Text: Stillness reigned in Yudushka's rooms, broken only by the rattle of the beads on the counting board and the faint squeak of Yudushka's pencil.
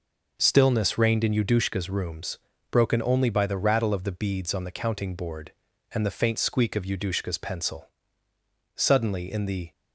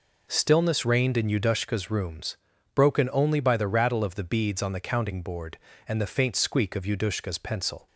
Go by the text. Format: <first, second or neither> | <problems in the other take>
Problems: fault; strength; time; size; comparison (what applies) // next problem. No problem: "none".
second | goes on to say "Suddenly in the"; noticeable; from 8.7 s on; 0.96 s long